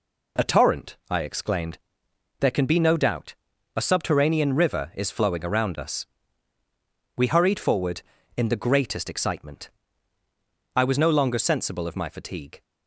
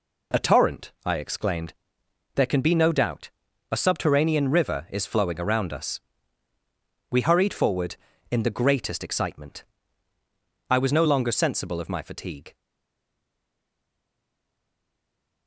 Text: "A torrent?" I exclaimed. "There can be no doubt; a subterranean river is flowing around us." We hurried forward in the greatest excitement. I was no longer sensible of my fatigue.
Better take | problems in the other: first | stays silent after the last word; strong; from 12.5 s on; 2.9 s long

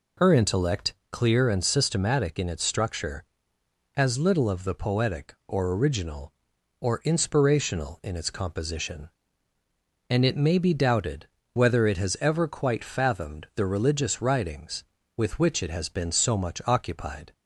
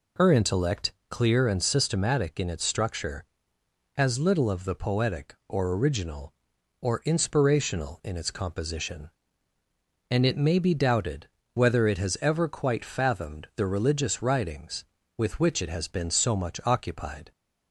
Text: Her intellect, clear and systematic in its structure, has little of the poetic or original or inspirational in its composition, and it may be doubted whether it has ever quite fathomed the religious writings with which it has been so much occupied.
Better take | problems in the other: neither | pauses between "doubted" and "whether"; slight; the same in both

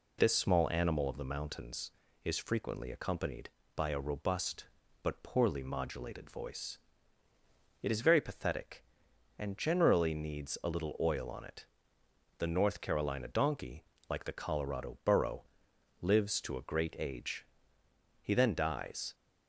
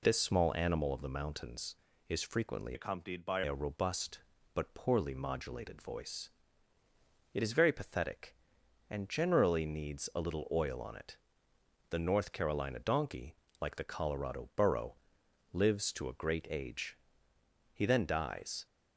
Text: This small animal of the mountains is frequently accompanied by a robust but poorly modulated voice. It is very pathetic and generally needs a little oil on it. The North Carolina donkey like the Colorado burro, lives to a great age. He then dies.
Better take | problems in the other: first | changes voice from "accompanied" to "by"; from 2.7 to 3.4 s; 0.7 s long // pauses between "donkey" and "like"; slight; at 13.3 s; 0.26 s long; slight in the first

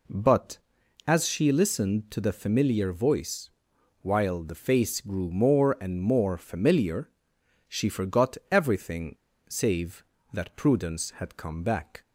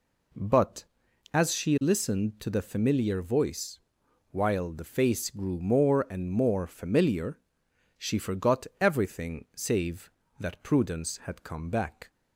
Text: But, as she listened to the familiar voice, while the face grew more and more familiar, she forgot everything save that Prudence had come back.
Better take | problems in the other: second | pauses between "everything" and "save"; slight; at 9.1 s; 0.32 s long

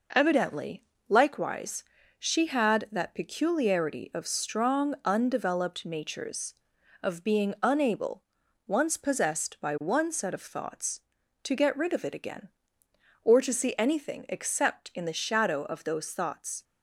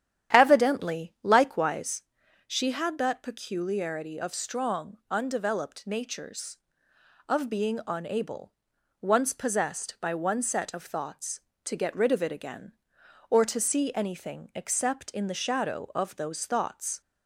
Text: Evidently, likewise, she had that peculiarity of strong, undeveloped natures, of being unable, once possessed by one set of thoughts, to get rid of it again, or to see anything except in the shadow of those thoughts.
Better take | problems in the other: first | starts louder than the rest; strong; until 1.9 s; 10 dB

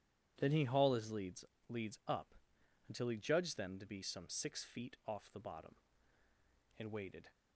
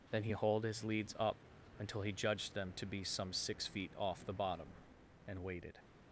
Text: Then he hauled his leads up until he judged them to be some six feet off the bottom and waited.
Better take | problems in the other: second | says "leads" twice; at 1.6 s // pauses between "up" and "until"; noticeable; at 2.3 s; 0.54 s long; also in the second

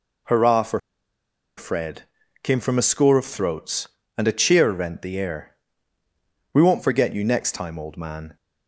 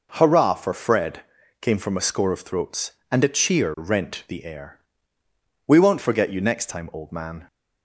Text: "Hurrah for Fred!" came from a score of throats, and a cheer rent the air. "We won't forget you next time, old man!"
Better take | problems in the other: second | pauses between "for" and "Fred"; noticeable; at 0.7 s; 0.78 s long

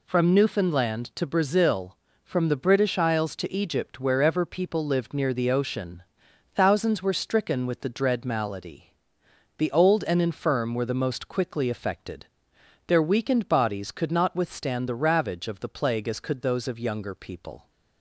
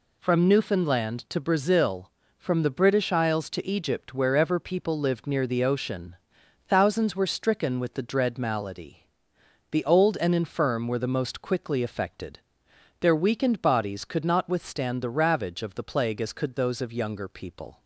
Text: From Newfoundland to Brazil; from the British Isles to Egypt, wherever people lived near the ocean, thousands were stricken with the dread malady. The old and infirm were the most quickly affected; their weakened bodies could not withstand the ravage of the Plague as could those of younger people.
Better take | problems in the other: neither | none

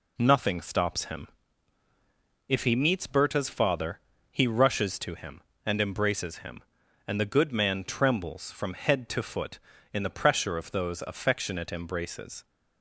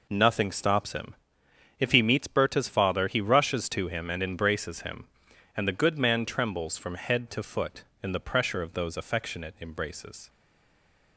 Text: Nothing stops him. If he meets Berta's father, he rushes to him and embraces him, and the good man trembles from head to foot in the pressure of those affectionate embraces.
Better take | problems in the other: first | stays silent after the last word; slight; from 10.2 s on; 0.9 s long

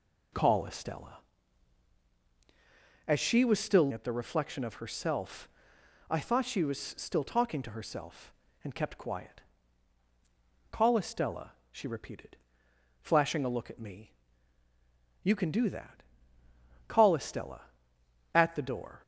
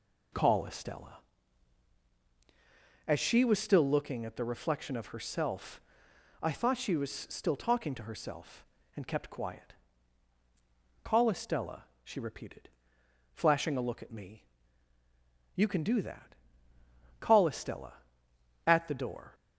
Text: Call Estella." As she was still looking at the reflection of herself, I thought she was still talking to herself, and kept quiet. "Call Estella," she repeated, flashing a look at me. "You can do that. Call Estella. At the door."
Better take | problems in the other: second | skips "looking"; at 3.9 s

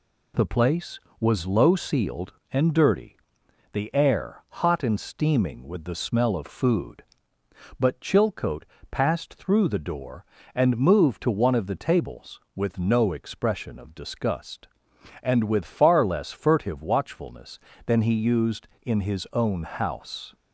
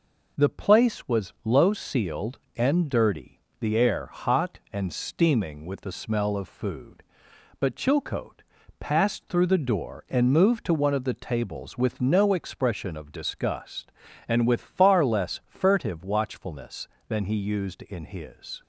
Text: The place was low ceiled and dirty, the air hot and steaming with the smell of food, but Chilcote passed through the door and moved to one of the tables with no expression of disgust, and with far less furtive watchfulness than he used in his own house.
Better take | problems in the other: first | pauses between "Chilcote" and "passed"; at 8.4 s; 0.38 s long; slight in the first // stops before "own house"; at 18.6 s

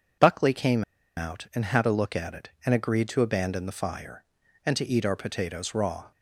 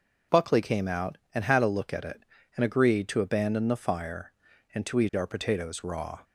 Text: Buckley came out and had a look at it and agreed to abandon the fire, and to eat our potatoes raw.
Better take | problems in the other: second | pauses between "came" and "out"; slight; at 0.8 s; 0.34 s long

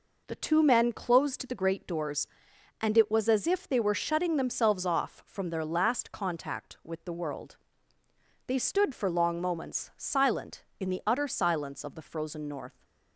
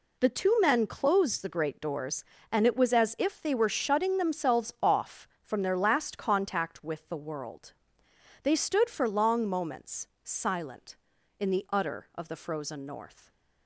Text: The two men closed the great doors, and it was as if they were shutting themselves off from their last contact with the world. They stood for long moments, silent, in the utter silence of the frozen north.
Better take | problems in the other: first | skips "silence"; at 12.1 s

